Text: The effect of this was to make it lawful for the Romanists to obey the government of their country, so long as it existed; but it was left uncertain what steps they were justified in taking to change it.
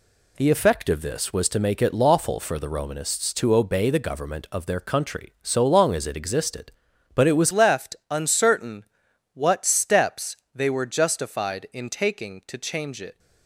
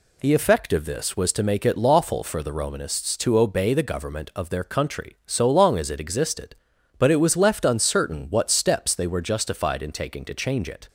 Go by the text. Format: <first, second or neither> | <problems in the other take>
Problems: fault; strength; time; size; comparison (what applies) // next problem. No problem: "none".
second | changes voice at "left"; from 7.5 s on; 5.6 s long // pauses between "uncertain" and "what"; noticeable; at 8.8 s; 0.50 s long // pauses between "steps" and "they"; slight; at 10.3 s; 0.18 s long